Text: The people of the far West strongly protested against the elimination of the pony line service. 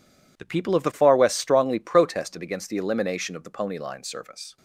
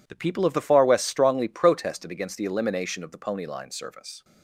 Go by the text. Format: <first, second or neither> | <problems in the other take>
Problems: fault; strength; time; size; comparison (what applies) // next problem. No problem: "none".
neither | none